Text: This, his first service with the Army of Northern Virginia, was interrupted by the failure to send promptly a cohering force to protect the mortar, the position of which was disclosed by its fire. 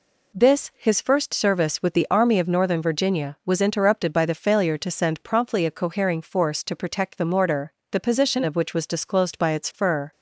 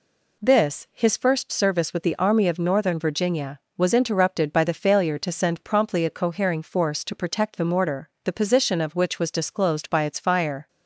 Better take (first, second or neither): second